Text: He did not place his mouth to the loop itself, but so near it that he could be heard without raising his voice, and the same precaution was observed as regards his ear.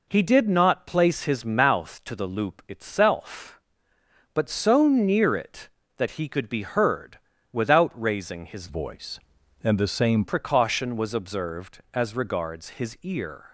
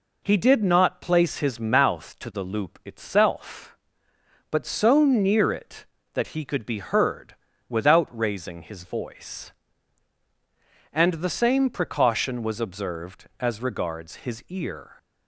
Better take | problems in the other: second | pauses between "heard" and "without"; slight; at 7.1 s; 0.34 s long; slight in the second // changes voice from "voice" to "same"; from 8.6 to 10.2 s; 1.6 s long

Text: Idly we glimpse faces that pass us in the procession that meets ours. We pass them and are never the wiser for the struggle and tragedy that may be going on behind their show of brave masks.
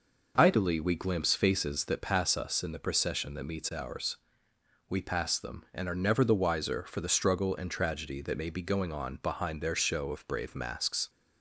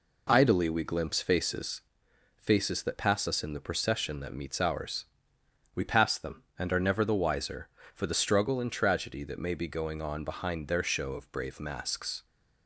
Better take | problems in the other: first | says "faces" twice; at 2.3 s

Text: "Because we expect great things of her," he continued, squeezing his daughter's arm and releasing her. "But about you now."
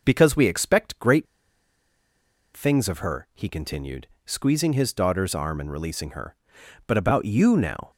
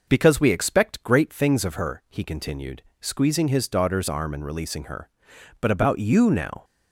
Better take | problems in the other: second | pauses between "great" and "things"; strong; at 1.2 s; 1.3 s long

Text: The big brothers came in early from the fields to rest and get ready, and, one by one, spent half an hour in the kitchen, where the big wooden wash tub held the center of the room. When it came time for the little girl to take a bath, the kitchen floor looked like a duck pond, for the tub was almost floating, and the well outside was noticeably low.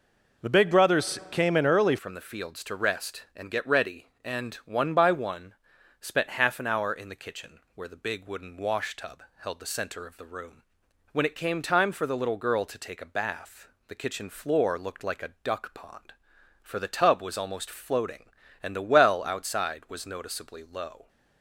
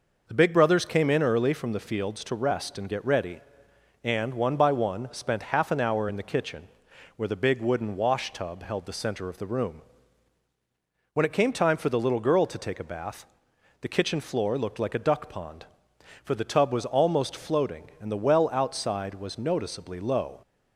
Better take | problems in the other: second | changes voice at "from"; from 1.9 s on; 19.1 s long // pauses between "tub" and "held"; slight; at 9.2 s; 0.16 s long

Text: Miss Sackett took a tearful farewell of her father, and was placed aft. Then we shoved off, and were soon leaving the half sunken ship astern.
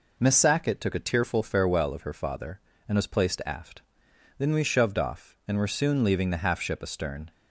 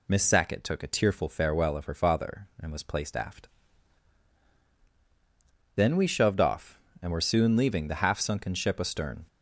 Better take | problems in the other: second | skips "sunken"; at 6.5 s

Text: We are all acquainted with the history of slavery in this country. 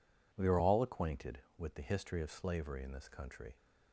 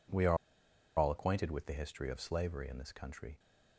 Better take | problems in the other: first | pauses between "are" and "all"; noticeable; at 0.3 s; 0.61 s long

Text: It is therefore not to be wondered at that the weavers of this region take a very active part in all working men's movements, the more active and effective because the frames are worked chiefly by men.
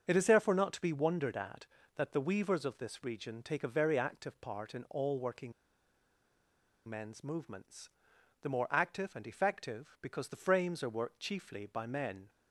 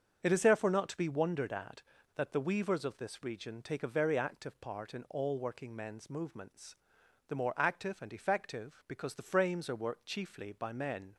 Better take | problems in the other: second | starts louder than the rest; until 1.1 s; 7 dB; also in the second // pauses between "working" and "men's"; strong; at 5.5 s; 1.3 s long

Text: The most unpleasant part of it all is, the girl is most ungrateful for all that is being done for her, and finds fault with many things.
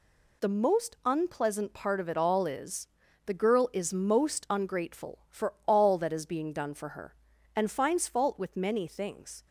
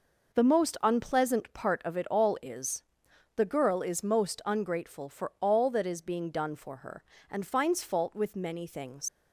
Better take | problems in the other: first | leaves "things" unfinished; at 9.0 s; 95 ms

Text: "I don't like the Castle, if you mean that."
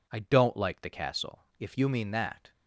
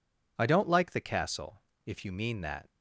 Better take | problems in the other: neither | none

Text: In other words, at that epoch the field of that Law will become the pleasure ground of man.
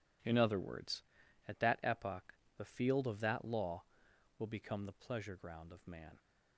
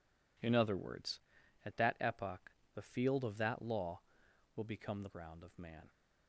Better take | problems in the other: first | pauses between "epoch" and "the"; slight; at 2.5 s; 0.24 s long; slight in the first // skips "pleasure"; at 5.0 s

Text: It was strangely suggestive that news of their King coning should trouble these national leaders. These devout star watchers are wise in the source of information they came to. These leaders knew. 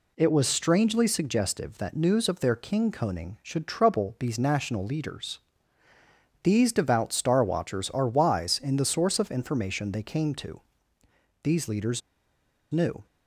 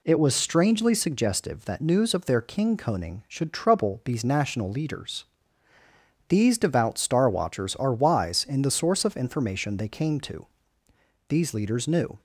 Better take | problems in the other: second | pauses between "leaders" and "knew"; noticeable; at 12.0 s; 0.70 s long

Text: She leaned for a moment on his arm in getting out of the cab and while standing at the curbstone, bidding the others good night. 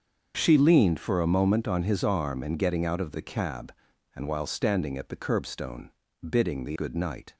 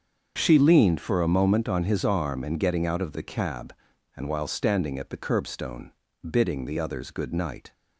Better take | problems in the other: second | starts louder than the rest; until 1.3 s; 6.5 dB; also in the second // skips "others"; at 6.7 s

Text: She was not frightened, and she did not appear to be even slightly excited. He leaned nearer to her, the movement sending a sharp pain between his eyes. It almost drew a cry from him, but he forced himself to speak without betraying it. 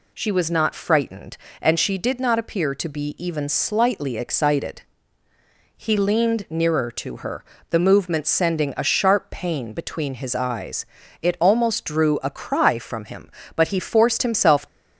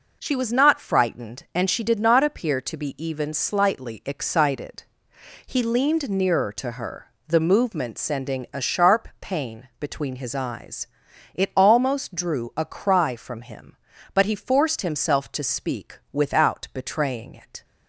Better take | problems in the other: second | stops before "to speak without betraying it"; at 14.6 s

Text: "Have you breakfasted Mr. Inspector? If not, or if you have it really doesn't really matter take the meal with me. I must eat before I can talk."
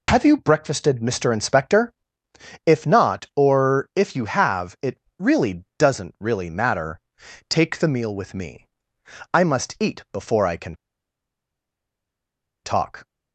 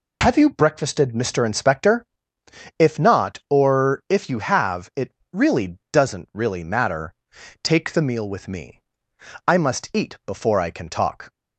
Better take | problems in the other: second | pauses between "it" and "really"; slight; at 4.9 s; 0.22 s long; slight in the second // pauses between "matter" and "take"; noticeable; at 6.9 s; 0.48 s long; noticeable in the second // pauses between "can" and "talk"; strong; at 10.7 s; 1.9 s long

